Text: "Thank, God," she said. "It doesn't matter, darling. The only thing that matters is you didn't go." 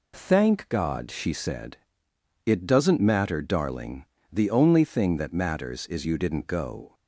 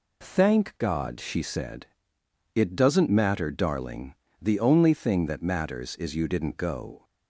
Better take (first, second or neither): neither